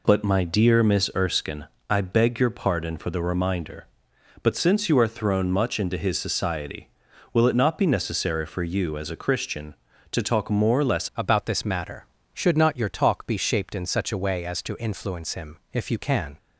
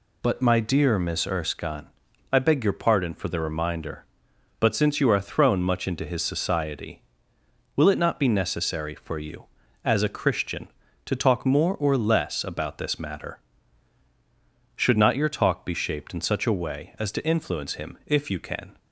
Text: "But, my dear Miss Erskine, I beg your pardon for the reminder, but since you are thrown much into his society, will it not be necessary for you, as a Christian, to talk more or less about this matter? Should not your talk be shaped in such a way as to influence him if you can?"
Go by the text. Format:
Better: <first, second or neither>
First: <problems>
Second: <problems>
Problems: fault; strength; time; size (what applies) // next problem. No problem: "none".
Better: second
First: changes voice at "about"; from 11.1 s on; 5.2 s long // pauses between "him" and "if"; slight; at 15.5 s; 0.16 s long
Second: none